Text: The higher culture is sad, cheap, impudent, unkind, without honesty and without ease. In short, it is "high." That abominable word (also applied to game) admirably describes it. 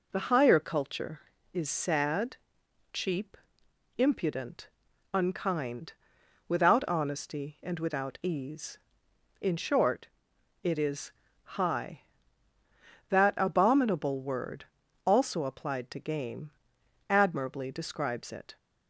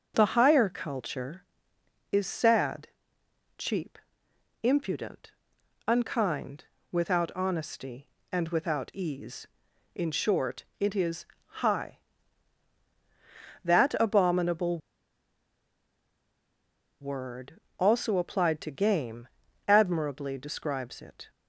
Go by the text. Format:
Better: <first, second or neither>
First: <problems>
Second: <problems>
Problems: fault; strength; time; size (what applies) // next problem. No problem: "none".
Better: first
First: pauses between "is" and "high"; slight; at 11.1 s; 0.32 s long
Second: pauses between "is" and "high"; slight; at 11.2 s; 0.34 s long // pauses between "abominable" and "word"; strong; at 14.7 s; 2.2 s long